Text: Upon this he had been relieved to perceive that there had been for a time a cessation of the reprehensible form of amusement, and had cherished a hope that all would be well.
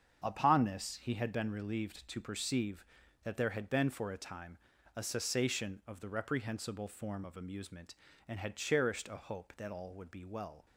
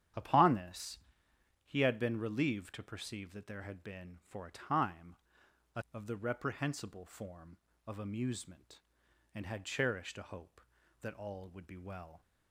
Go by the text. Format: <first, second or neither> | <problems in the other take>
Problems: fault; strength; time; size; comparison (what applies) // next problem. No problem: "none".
first | starts louder than the rest; strong; until 1.8 s; 10 dB; strong in the first // pauses between "this" and "he"; noticeable; at 0.9 s; 0.68 s long // pauses between "time" and "a"; noticeable; at 5.1 s; 0.58 s long; also in the first // skips "cessation"; at 5.8 s